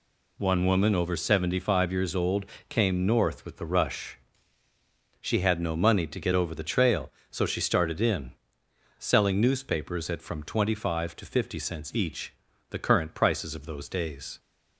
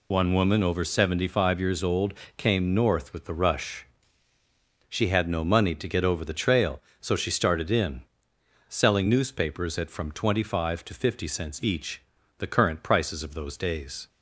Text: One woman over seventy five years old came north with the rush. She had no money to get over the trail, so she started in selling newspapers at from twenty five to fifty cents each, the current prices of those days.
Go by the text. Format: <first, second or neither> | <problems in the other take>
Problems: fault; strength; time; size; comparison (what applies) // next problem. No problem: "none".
first | loses the start of "One"; at 0.1 s; 45 ms // pauses between "old" and "came"; slight; at 2.1 s; 0.24 s long; slight in the first // pauses between "in" and "selling"; noticeable; at 8.0 s; 0.66 s long; noticeable in the first